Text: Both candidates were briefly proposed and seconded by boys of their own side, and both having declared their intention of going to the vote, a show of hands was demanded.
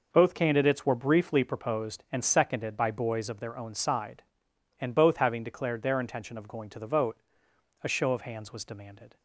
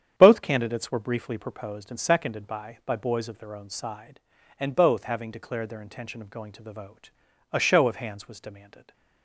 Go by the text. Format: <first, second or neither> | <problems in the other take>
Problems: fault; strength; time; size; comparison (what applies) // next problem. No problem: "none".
first | starts louder than the rest; strong; until 1.1 s; 8.5 dB // says "by" twice; at 2.8 s